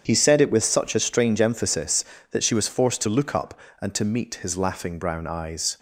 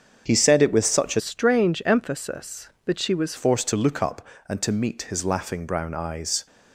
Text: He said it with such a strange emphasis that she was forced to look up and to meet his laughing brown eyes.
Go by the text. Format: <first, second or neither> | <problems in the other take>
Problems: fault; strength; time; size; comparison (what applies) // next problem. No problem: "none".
first | starts louder than the rest; strong; until 1.2 s; 7 dB; strong in the first // changes voice from "strange" to "was"; from 1.1 to 3.3 s; 2.2 s long